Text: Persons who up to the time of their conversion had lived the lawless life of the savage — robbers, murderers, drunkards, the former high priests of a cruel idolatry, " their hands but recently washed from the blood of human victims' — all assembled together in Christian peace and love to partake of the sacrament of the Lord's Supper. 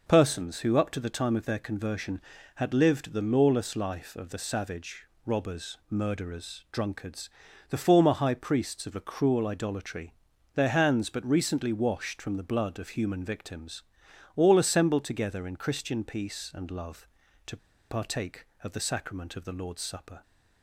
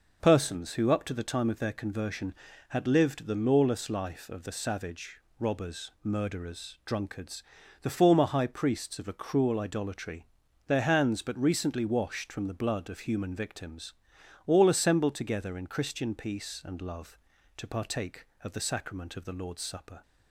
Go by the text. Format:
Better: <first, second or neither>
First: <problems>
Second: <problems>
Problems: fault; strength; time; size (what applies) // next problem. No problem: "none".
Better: second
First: pauses between "to" and "partake"; slight; at 17.5 s; 0.32 s long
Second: none